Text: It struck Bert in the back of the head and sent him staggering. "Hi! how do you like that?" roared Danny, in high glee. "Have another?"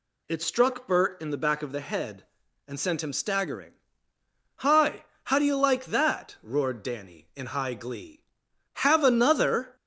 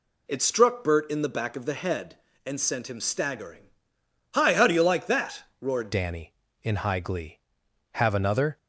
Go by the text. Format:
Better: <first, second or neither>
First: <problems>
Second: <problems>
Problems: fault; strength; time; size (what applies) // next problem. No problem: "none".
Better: first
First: none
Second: changes voice at "Danny"; from 5.9 s on; 2.6 s long